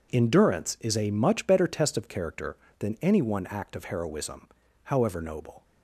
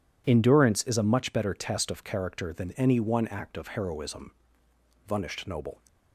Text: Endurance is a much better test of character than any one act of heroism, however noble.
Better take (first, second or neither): first